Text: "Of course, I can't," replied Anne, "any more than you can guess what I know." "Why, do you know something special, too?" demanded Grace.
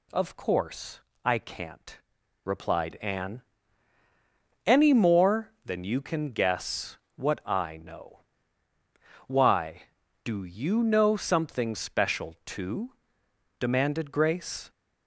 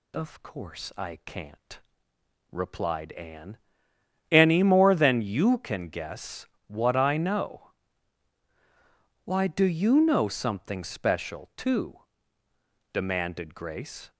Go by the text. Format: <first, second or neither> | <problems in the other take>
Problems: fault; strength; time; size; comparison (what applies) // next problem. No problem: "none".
neither | pauses between "guess" and "what"; slight; the same in both